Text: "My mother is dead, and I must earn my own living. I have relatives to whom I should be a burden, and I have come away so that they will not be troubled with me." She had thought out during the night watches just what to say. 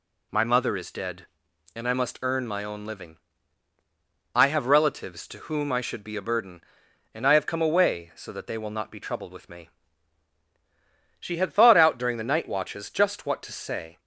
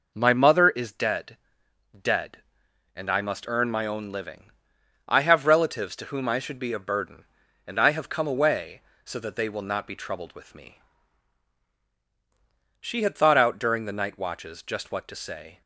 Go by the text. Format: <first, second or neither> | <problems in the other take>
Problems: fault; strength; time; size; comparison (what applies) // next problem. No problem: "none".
first | says "dead" twice; at 1.9 s